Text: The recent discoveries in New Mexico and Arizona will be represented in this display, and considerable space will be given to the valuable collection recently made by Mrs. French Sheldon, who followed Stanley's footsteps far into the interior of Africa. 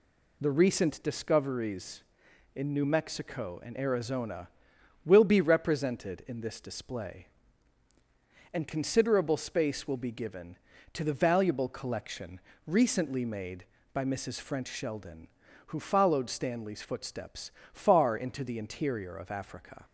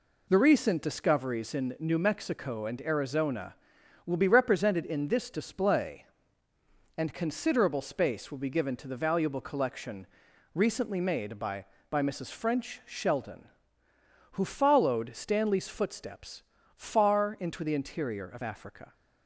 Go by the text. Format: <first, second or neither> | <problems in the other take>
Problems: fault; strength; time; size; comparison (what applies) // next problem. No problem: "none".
first | pauses between "collection" and "recently"; noticeable; at 10.0 s; 0.48 s long; slight in the first // says "by" twice; at 11.8 s // pauses between "footsteps" and "far"; slight; at 16.4 s; 0.32 s long; slight in the first